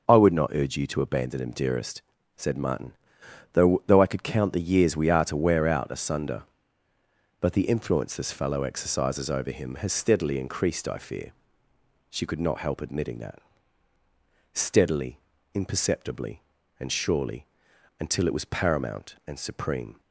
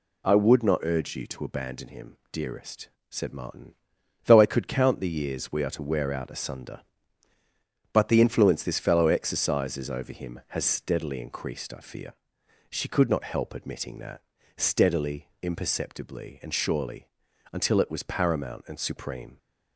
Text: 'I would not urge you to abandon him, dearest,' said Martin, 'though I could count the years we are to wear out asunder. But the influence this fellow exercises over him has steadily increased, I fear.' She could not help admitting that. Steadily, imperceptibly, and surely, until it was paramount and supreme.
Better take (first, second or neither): second